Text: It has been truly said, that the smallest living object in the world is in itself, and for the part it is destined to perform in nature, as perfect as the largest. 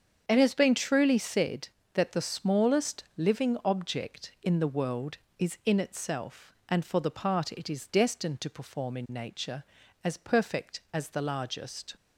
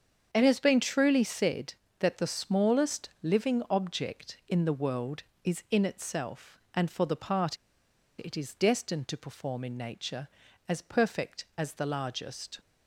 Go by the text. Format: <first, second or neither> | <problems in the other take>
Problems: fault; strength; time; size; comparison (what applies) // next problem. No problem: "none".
first | starts louder than the rest; strong; until 1.3 s; 7.5 dB; strong in the first // pauses between "part" and "it"; noticeable; at 7.5 s; 0.63 s long